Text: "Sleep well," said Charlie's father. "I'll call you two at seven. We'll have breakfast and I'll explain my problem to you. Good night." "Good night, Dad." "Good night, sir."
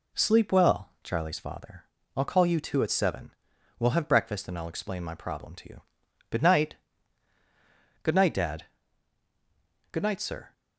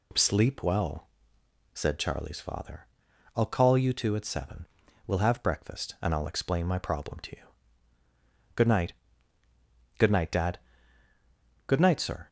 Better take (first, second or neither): second